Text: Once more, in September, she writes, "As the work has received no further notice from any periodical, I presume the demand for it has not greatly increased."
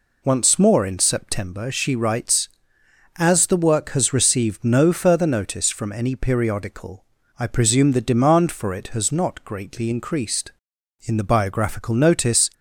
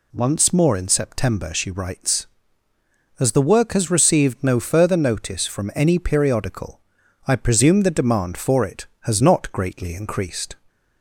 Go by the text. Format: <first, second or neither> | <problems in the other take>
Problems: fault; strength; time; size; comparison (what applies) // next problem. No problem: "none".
second | goes on to say "In the biographical notice"; from 11.0 s on; 1.4 s long